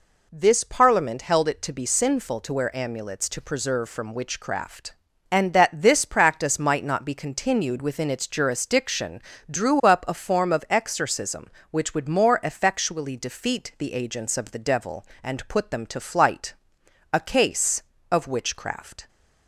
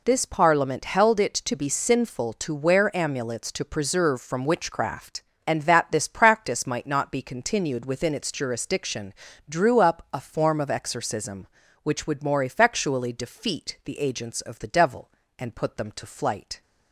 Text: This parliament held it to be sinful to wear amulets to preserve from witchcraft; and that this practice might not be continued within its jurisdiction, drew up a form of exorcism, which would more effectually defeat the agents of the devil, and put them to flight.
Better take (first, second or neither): second